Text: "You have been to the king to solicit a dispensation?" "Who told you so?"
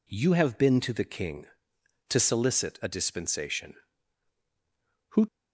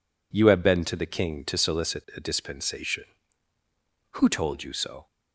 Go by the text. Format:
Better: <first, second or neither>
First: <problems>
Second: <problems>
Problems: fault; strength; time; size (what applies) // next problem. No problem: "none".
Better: second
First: stops before "told you so"; at 5.2 s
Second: none